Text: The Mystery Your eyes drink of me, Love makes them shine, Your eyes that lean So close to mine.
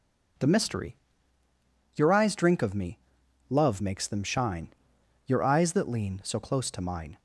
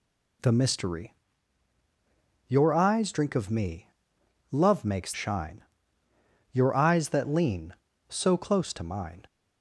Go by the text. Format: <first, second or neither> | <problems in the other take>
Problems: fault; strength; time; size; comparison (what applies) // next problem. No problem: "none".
first | pauses between "Mystery" and "Your"; strong; at 1.1 s; 1.3 s long; noticeable in the first // skips "them"; at 5.1 s